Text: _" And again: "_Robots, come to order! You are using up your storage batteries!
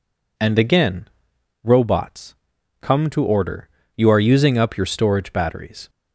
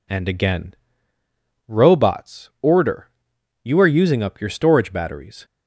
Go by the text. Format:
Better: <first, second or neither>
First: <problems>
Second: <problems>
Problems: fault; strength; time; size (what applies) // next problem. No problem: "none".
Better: first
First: none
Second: skips "come to"; at 2.5 s